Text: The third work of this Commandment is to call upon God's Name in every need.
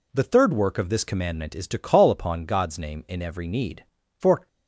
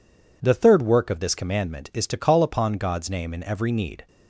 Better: second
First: goes on to say "For"; slight; from 4.1 s on; 0.30 s long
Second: none

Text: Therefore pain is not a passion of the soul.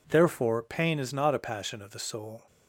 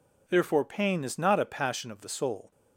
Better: neither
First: none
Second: none

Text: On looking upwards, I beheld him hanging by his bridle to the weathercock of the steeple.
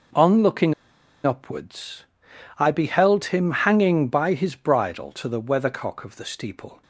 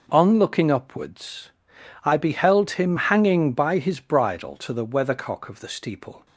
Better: second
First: pauses between "looking" and "upwards"; noticeable; at 0.7 s; 0.52 s long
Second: none

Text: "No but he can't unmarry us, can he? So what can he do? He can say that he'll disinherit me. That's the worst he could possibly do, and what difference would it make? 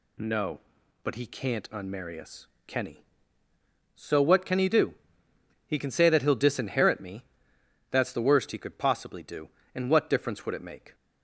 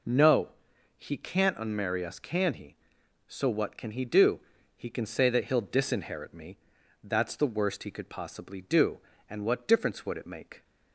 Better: first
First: none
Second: skips "but"; at 0.7 s

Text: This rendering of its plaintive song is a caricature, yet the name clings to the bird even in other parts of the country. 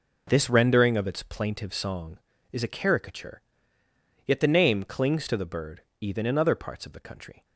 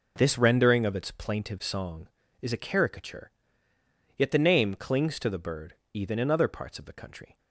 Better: neither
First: pauses between "bird" and "even"; slight; at 5.8 s; 0.18 s long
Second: pauses between "bird" and "even"; slight; at 5.7 s; 0.18 s long

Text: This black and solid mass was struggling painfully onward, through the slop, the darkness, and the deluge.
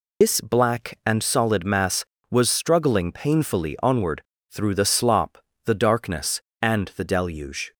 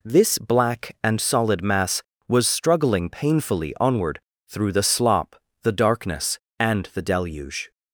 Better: second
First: loses the start of "This"; at 0.2 s; 155 ms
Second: none

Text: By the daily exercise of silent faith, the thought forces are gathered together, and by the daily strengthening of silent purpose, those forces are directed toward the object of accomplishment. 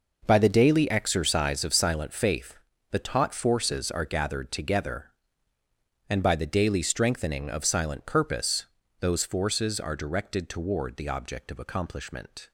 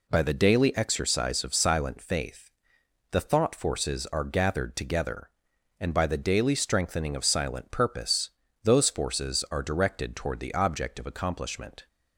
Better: second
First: says "taught" for "thought"; at 2.9 s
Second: none

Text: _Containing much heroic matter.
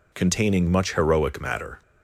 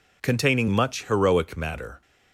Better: neither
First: none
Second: none

